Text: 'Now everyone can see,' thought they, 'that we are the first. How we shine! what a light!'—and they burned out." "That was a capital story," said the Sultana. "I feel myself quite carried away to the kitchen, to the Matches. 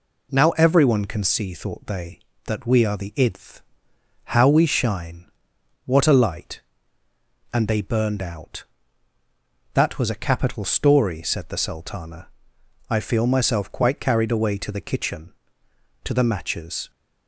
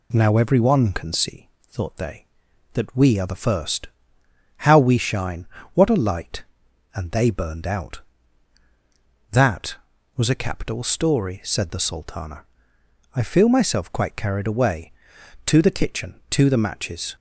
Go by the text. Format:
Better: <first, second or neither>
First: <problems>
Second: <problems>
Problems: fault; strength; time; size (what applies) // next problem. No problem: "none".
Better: second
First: says "idth" for "first"; at 3.1 s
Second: none